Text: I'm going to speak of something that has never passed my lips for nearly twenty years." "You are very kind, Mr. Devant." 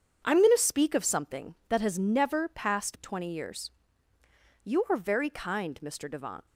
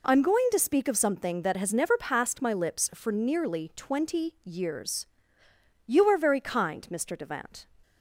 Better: second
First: starts louder than the rest; strong; until 1.2 s; 7.5 dB // skips "my lips for nearly"; at 2.9 s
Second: none

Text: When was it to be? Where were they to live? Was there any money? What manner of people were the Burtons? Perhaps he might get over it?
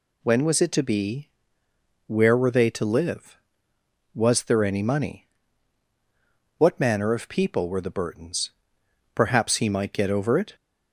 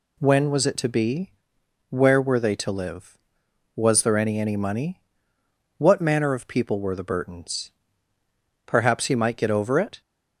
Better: first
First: none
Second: says "any" twice; at 4.4 s

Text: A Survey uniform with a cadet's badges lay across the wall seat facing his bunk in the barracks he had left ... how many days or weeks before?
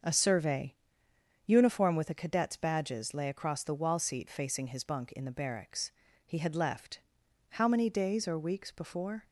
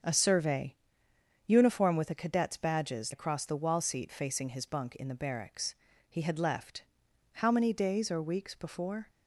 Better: first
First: starts louder than the rest; until 1.7 s; 6.5 dB // pauses between "Survey" and "uniform"; noticeable; at 0.7 s; 0.72 s long // pauses between "barracks" and "he"; slight; at 5.9 s; 0.36 s long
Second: starts louder than the rest; strong; until 1.7 s; 7 dB // pauses between "Survey" and "uniform"; noticeable; at 0.7 s; 0.72 s long // skips "lay"; at 3.1 s // pauses between "barracks" and "he"; slight; at 5.7 s; 0.36 s long

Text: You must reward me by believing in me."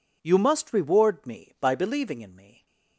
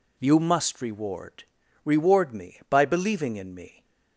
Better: first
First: none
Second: says "reward" twice; at 1.8 s

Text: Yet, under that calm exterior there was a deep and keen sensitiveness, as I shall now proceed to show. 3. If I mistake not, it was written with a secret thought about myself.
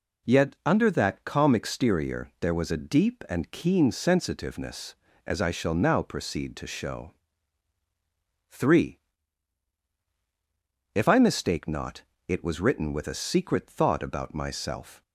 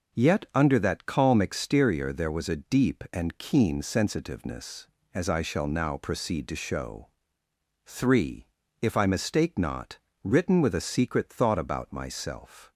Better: first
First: none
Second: skips "it was"; at 10.1 s

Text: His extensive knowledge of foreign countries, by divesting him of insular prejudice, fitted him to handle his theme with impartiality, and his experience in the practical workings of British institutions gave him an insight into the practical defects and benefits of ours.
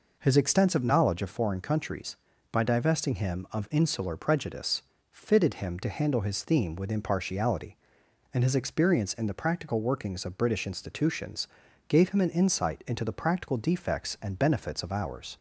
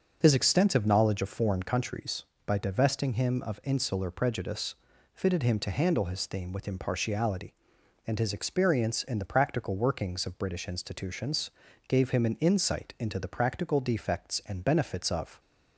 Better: first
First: pauses between "institutions" and "gave"; at 11.4 s; 0.40 s long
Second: pauses between "institutions" and "gave"; at 11.4 s; 0.38 s long // stops before "ours"; at 15.3 s

